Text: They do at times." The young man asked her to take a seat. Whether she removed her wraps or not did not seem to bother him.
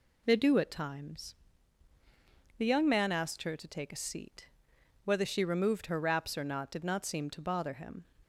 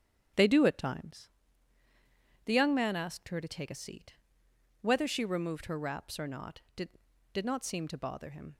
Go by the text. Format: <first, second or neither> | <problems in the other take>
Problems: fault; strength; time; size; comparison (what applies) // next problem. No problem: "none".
first | starts louder than the rest; strong; until 2.5 s; 8.5 dB // says "did" twice; at 7.3 s